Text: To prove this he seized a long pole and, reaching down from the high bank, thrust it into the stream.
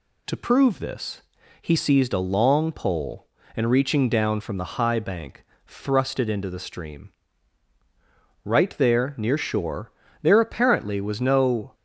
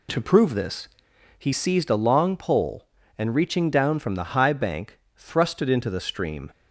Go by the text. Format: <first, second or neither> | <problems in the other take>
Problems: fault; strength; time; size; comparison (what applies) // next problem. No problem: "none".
second | pauses between "this" and "he"; at 1.2 s; 0.40 s long; noticeable in the second // goes on to say "Right there near shore there apparently was no"; strong; from 8.4 s on; 3.3 s long